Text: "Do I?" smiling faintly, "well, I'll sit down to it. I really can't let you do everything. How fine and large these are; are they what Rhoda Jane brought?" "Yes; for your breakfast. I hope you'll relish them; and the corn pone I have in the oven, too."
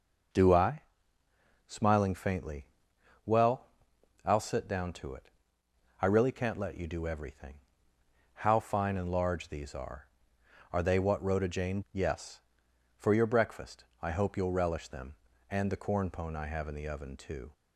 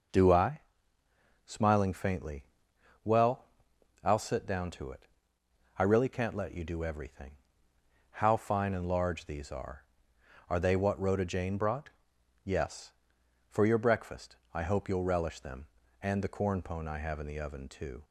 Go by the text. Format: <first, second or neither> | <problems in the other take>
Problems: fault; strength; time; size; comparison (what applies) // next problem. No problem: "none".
second | skips "brought"; at 11.8 s